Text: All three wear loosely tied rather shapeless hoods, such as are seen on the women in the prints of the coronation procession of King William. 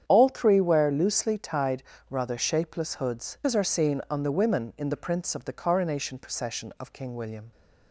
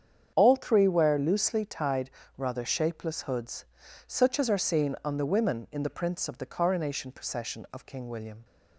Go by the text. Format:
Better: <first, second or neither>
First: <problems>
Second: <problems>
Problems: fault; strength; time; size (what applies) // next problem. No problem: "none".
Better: second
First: starts louder than the rest; strong; until 1.0 s; 8.5 dB // pauses between "tied" and "rather"; slight; at 1.8 s; 0.26 s long // skips "such"; at 3.4 s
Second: starts louder than the rest; strong; until 1.3 s; 8 dB // pauses between "tied" and "rather"; slight; at 2.1 s; 0.26 s long